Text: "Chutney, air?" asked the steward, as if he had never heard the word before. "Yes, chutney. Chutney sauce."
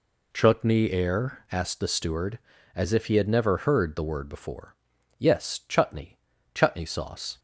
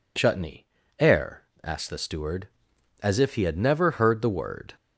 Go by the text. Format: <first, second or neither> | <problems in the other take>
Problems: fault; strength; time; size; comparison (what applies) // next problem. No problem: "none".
first | stops before "before Yes chutney Chutney sauce"; at 4.7 s